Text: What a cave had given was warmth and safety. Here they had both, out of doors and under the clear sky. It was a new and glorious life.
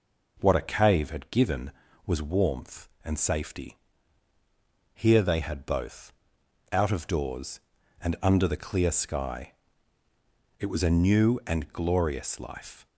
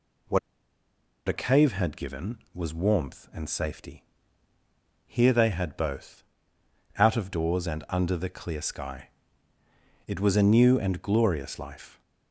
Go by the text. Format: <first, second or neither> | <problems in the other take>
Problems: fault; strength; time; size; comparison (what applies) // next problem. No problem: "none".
first | pauses between "What" and "a"; noticeable; at 0.3 s; 0.89 s long